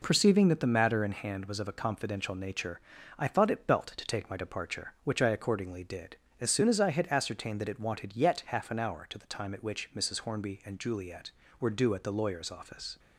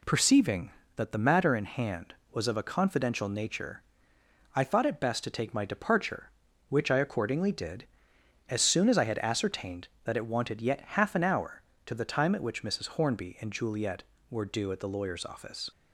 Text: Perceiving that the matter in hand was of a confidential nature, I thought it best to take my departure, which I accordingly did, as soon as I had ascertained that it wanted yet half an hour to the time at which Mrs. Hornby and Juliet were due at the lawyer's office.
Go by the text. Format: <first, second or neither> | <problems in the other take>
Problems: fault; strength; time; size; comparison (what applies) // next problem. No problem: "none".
second | says "belt" for "best"; at 3.6 s